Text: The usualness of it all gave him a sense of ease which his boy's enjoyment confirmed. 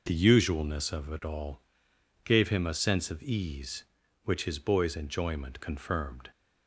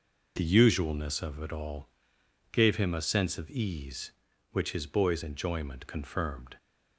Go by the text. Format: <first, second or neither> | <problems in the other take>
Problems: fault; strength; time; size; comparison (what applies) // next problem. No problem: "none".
neither | pauses between "all" and "gave"; noticeable; the same in both